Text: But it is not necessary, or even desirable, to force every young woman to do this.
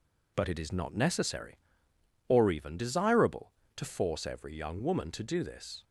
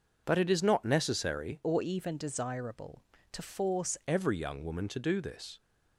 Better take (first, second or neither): first